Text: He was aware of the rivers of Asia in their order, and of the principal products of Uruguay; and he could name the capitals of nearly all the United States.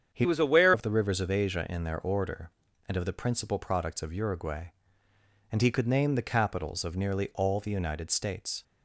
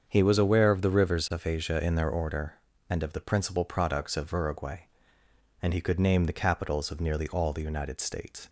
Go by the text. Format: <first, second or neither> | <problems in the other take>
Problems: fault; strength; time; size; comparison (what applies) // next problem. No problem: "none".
second | starts louder than the rest; strong; until 1.1 s; 8 dB; also in the second // changes voice from "was" to "aware"; from 0.2 to 0.7 s; 0.5 s long